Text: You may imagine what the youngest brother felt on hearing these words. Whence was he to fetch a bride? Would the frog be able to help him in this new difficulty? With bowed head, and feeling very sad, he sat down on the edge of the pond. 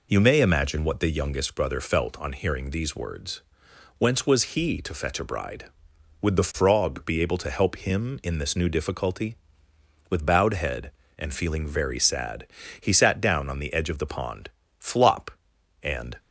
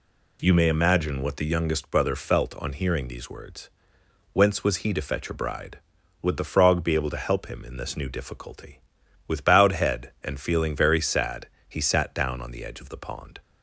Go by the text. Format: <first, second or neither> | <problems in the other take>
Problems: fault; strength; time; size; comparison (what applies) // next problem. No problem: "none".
second | goes on to say "Flop and"; from 14.7 s on; 1.3 s long